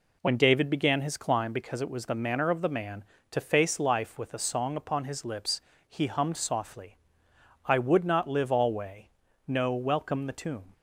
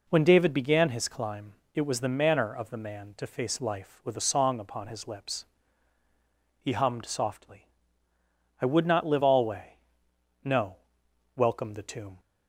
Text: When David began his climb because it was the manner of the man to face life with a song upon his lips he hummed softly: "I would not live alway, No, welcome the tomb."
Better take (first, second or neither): first